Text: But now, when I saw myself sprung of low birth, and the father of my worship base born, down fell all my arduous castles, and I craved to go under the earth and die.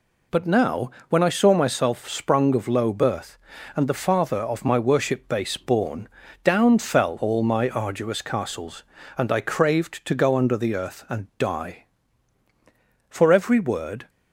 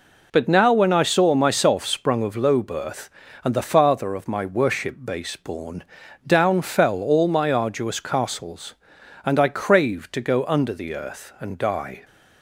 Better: second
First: pauses between "and" and "die"; slight; at 11.2 s; 0.16 s long // goes on to say "For every word"; noticeable; from 13.0 s on; 1.0 s long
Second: none

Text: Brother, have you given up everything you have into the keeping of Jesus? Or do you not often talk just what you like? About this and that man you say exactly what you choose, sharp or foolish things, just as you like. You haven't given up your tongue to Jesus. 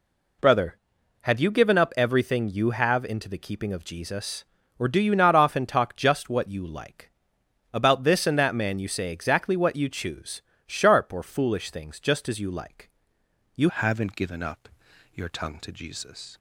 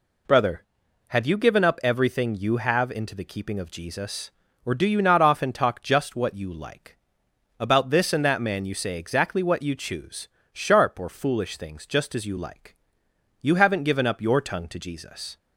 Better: second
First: changes voice at "haven't"; from 13.6 s on; 2.7 s long // pauses between "up" and "your"; noticeable; at 14.6 s; 0.46 s long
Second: none

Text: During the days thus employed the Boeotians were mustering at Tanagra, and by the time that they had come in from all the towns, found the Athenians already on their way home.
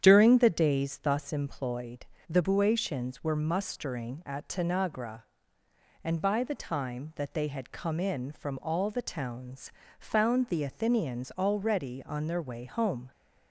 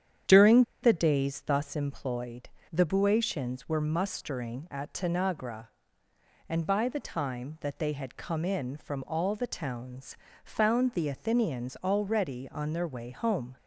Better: first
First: starts louder than the rest; strong; until 1.0 s; 9 dB // pauses between "employed" and "the"; slight; at 2.0 s; 0.24 s long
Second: starts louder than the rest; strong; until 1.4 s; 9 dB // pauses between "During" and "the"; slight; at 0.6 s; 0.20 s long // pauses between "employed" and "the"; slight; at 2.4 s; 0.24 s long

